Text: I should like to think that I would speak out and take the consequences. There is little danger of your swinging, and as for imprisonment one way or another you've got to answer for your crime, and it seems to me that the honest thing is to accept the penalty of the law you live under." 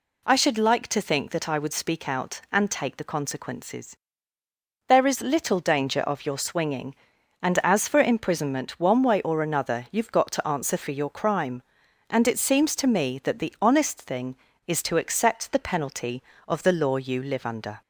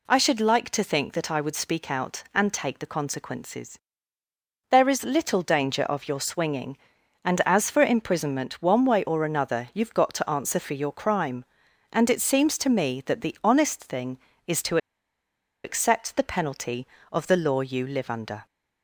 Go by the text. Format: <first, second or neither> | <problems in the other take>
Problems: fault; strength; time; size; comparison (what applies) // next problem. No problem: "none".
first | pauses between "to" and "accept"; noticeable; at 14.7 s; 0.87 s long